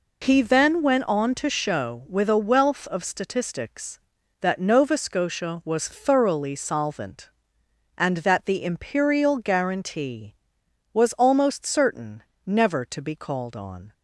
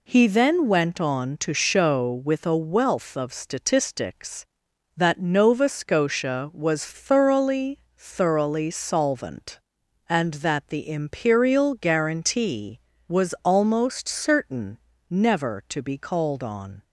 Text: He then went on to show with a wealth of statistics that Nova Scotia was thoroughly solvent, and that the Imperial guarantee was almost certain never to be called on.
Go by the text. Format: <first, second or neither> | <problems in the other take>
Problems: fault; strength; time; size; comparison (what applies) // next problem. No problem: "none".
first | says "thoroughly" twice; at 7.9 s // pauses between "certain" and "never"; slight; at 14.7 s; 0.32 s long; slight in the first